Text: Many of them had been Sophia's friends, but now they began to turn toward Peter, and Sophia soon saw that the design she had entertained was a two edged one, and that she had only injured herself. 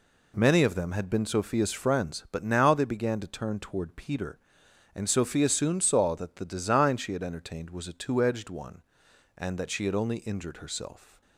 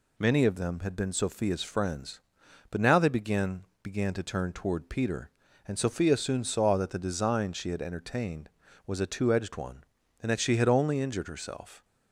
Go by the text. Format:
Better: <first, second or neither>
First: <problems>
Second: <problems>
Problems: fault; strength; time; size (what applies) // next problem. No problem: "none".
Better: first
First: none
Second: says "began" twice; at 3.8 s